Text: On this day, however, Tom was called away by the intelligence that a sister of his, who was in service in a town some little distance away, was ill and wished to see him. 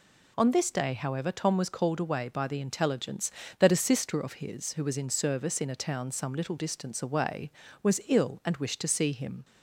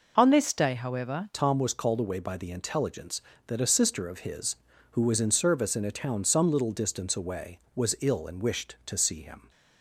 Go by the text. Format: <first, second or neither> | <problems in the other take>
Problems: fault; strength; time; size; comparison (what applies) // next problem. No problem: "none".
first | changes voice at "Tom"; from 1.3 s on; 8.1 s long